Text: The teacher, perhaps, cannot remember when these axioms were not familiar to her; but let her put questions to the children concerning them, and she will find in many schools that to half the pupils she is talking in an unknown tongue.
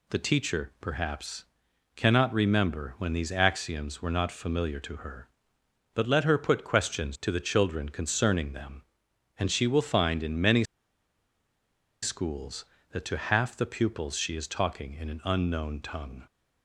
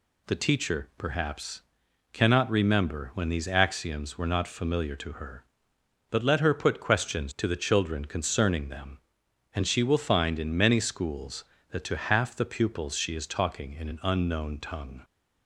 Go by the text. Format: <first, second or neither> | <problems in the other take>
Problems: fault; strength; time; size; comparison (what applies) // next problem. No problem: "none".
second | pauses between "many" and "schools"; strong; at 10.6 s; 1.3 s long